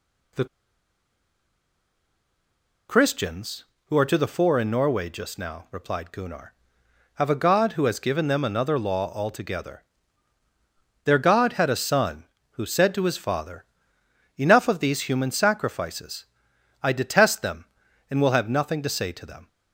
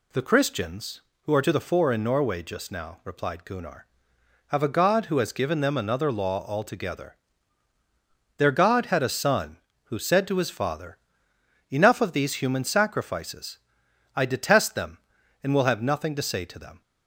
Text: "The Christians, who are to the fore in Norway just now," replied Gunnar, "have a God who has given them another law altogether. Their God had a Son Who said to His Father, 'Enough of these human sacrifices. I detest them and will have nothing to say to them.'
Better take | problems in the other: second | pauses between "The" and "Christians"; strong; at 0.4 s; 2.4 s long

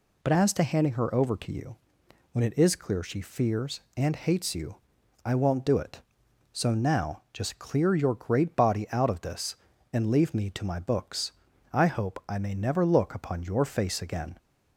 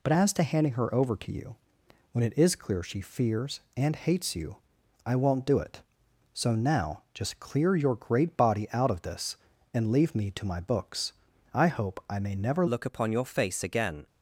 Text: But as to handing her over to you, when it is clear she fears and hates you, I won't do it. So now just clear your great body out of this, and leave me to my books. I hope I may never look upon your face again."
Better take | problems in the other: first | changes voice at "look"; from 12.6 s on; 1.4 s long

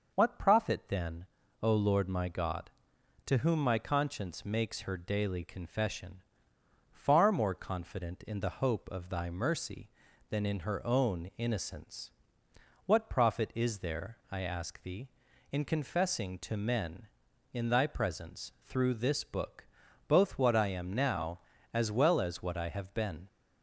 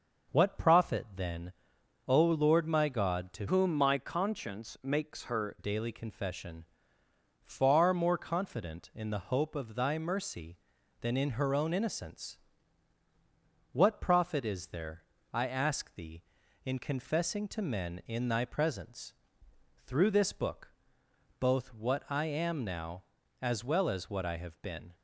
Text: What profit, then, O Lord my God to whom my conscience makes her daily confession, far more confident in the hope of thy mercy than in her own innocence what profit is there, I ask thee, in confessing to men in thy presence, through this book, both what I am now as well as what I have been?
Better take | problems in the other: first | changes voice from "whom" to "her"; from 3.4 to 5.5 s; 2.1 s long // pauses between "innocence" and "what"; strong; at 12.3 s; 1.3 s long; noticeable in the first

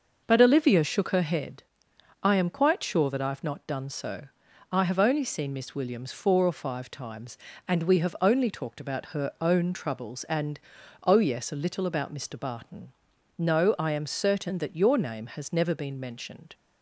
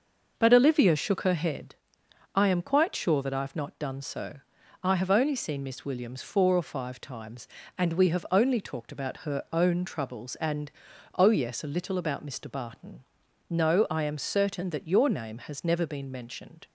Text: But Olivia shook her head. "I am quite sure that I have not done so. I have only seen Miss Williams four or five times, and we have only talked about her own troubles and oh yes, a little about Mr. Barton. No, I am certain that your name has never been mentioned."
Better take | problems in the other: neither | pauses between "and" and "oh"; noticeable; the same in both

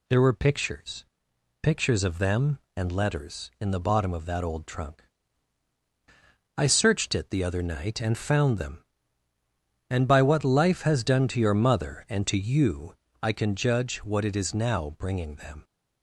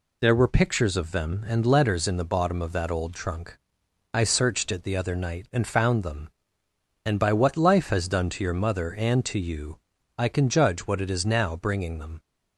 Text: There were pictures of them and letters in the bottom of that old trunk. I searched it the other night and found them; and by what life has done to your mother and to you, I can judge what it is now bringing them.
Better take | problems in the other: second | says "pictures" twice; at 1.6 s

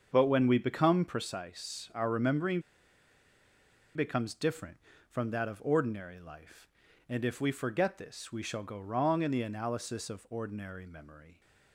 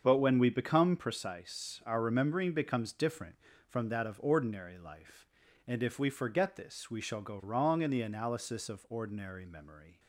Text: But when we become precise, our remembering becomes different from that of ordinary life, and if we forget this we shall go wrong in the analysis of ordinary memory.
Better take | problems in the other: second | starts louder than the rest; until 1.1 s; 7 dB; also in the second // pauses between "remembering" and "becomes"; strong; at 2.6 s; 1.3 s long

